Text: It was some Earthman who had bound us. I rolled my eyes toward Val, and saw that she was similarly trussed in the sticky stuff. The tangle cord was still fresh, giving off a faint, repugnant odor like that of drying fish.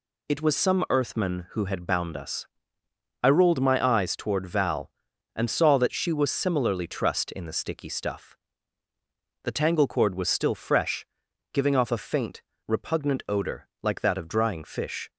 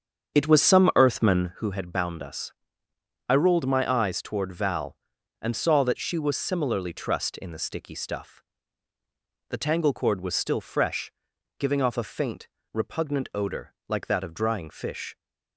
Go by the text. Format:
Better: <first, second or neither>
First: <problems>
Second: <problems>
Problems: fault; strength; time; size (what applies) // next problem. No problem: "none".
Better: first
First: none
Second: starts louder than the rest; strong; until 1.7 s; 7.5 dB